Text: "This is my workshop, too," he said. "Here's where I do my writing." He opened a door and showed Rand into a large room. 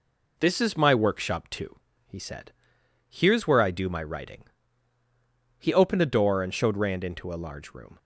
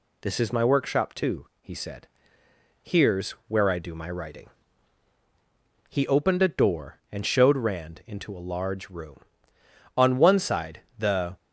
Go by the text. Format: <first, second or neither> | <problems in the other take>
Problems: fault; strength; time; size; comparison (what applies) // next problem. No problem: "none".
first | pauses between "Here's" and "where"; slight; at 3.3 s; 0.16 s long // goes on to say "On one side the"; from 9.9 s on; 1.4 s long